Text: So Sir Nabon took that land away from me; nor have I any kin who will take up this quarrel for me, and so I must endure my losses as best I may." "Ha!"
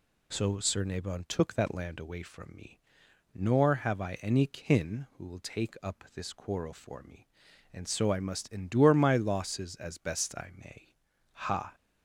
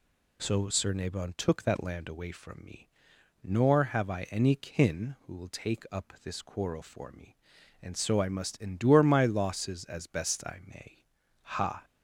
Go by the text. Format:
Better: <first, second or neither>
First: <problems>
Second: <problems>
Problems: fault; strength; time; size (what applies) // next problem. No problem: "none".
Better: neither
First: none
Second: none